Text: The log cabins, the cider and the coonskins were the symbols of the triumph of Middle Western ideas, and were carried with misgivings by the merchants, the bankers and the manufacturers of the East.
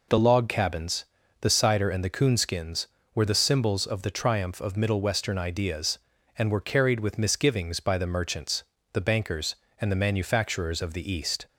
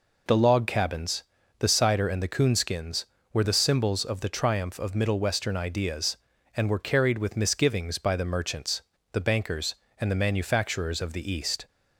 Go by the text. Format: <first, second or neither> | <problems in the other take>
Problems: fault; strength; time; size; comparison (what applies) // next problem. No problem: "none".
neither | none